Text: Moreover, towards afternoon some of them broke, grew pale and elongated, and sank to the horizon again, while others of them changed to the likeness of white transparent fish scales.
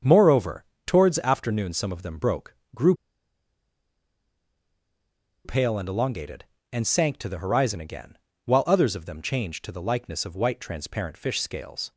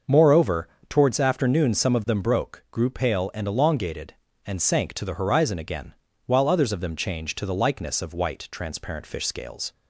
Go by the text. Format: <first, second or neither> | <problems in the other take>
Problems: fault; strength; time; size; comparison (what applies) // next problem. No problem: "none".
second | starts louder than the rest; until 1.2 s; 7 dB; noticeable in the second // pauses between "grew" and "pale"; strong; at 2.9 s; 2.5 s long